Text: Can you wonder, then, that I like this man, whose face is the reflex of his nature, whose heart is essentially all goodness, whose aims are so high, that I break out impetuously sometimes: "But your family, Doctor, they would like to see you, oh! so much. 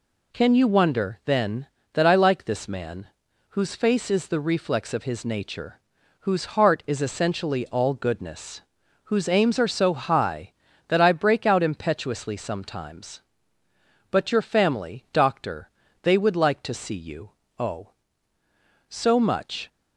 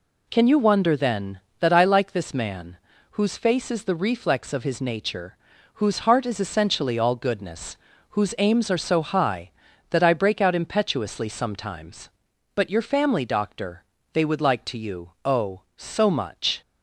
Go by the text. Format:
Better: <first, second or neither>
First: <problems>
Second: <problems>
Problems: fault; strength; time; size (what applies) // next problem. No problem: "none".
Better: first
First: none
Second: skips "see"; at 14.7 s